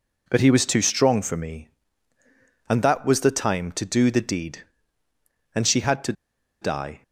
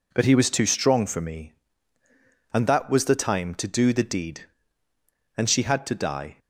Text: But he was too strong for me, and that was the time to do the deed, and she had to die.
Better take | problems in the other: second | pauses between "to" and "die"; noticeable; at 6.1 s; 0.49 s long

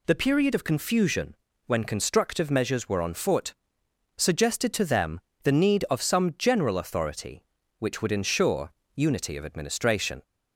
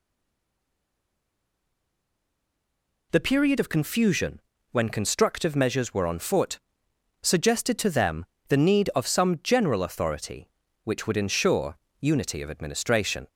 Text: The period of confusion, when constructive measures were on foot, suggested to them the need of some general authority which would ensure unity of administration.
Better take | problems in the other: first | stays silent before the first word; strong; until 3.1 s; 3.1 s long // pauses between "them" and "the"; slight; at 8.2 s; 0.24 s long; slight in the first // pauses between "ensure" and "unity"; slight; at 11.7 s; 0.24 s long; slight in the first

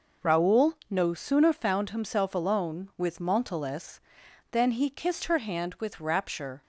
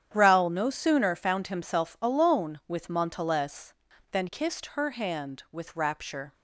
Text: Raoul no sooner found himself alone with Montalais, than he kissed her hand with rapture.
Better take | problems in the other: first | starts louder than the rest; strong; until 1.1 s; 9 dB // skips "he"; at 4.2 s

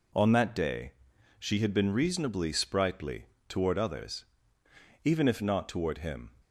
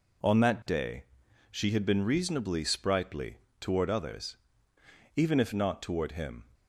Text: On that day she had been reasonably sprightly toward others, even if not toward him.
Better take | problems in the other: neither | pauses between "day" and "she"; noticeable; the same in both // pauses between "sprightly" and "toward"; slight; the same in both

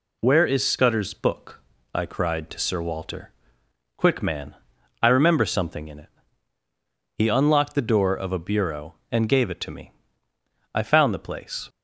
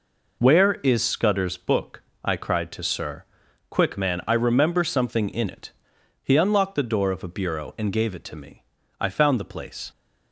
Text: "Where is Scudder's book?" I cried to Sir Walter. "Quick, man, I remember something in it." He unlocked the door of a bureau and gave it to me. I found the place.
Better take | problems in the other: first | skips "Walter"; at 3.4 s

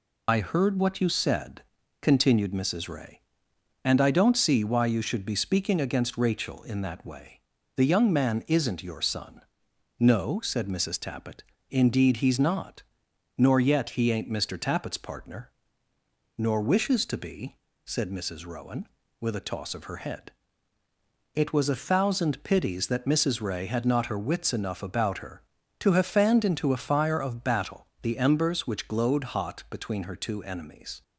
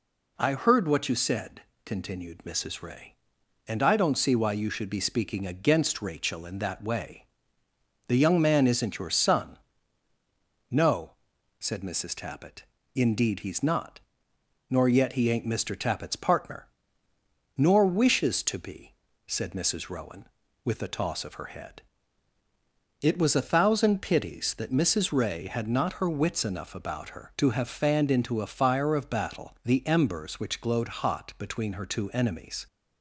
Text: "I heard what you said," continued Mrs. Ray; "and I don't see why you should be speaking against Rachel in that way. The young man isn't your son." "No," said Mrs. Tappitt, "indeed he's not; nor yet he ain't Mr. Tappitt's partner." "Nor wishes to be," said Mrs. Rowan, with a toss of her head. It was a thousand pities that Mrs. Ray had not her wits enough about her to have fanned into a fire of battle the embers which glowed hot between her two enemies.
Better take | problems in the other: second | loses the start of "I"; at 0.2 s; 40 ms // pauses between "battle" and "the"; slight; at 27.8 s; 0.16 s long

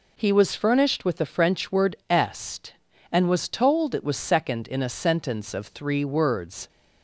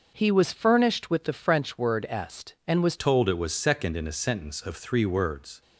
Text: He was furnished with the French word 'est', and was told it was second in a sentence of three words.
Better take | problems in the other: first | starts louder than the rest; noticeable; until 1.1 s; 6 dB // changes voice at "told"; from 2.9 s on; 2.7 s long

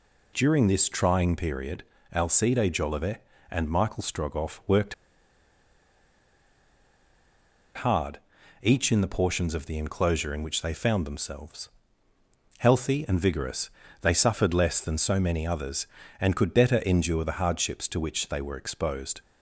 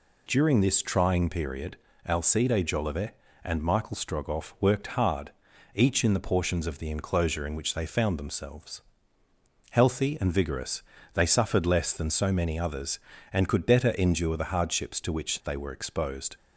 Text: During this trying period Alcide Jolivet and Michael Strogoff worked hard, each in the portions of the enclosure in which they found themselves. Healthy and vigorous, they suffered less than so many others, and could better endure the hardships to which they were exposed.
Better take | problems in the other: second | pauses between "period" and "Alcide"; slight; at 1.8 s; 0.28 s long; slight in the second // pauses between "worked" and "hard"; strong; at 4.9 s; 2.8 s long

